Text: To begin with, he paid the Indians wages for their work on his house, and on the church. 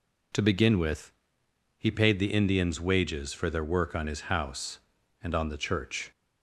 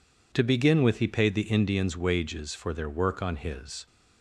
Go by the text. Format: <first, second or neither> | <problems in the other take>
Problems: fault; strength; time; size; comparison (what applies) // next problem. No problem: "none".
first | stops before "house and on the church"; at 3.8 s